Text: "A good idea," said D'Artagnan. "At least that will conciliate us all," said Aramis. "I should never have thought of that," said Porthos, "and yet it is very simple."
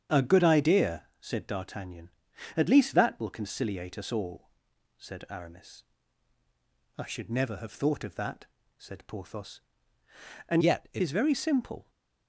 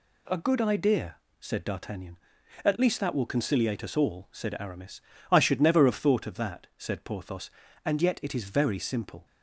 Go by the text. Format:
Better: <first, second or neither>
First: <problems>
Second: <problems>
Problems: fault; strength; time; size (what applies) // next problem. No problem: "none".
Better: second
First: starts louder than the rest; strong; until 1.2 s; 7.5 dB // changes voice from "yet" to "it"; from 10.6 to 11.0 s; 0.4 s long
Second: none